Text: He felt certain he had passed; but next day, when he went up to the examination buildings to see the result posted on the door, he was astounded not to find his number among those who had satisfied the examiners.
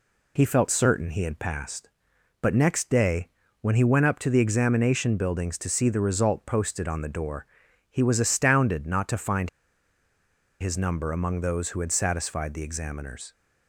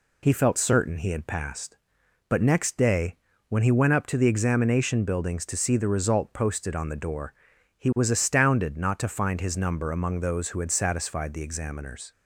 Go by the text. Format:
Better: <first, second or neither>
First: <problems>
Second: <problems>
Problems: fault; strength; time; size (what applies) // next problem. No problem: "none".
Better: second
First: pauses between "find" and "his"; at 9.4 s; 1.1 s long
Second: none